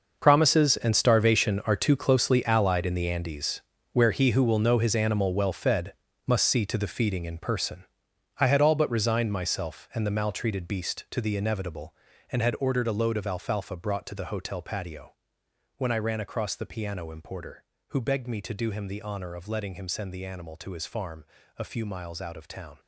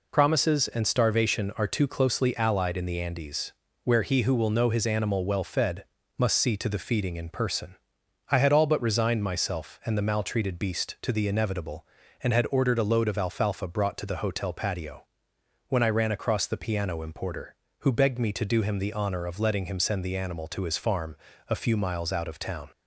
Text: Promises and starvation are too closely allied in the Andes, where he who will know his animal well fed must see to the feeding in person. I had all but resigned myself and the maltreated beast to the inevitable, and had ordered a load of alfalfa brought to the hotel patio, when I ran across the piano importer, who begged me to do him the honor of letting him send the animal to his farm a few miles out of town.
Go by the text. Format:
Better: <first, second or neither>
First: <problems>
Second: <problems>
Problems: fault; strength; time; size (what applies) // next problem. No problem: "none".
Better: second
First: gets quieter; strong; throughout; 13.5 dB // pauses between "fed" and "must"; slight; at 5.9 s; 0.32 s long // pauses between "farm" and "a"; slight; at 21.2 s; 0.34 s long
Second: pauses between "fed" and "must"; slight; at 5.8 s; 0.32 s long // pauses between "farm" and "a"; slight; at 21.1 s; 0.34 s long